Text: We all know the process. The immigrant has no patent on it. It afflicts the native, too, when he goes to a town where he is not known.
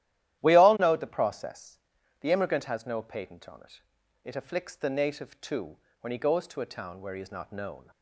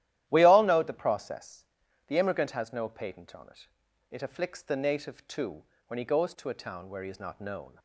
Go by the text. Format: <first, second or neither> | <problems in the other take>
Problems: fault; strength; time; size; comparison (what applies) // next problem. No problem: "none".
neither | starts louder than the rest; strong; the same in both